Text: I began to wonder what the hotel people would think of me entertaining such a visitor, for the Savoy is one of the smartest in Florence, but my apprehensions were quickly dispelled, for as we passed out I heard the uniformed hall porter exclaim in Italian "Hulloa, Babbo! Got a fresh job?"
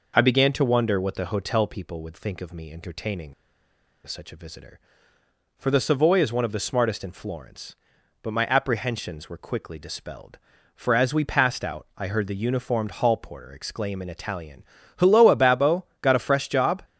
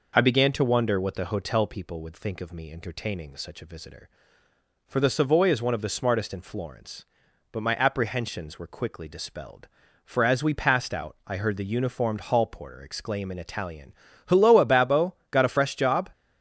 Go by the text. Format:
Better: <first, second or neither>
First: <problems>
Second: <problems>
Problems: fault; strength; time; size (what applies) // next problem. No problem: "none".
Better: second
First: pauses between "entertaining" and "such"; noticeable; at 3.3 s; 0.73 s long // pauses between "Italian" and "Hulloa"; slight; at 14.6 s; 0.36 s long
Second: pauses between "Italian" and "Hulloa"; slight; at 13.9 s; 0.36 s long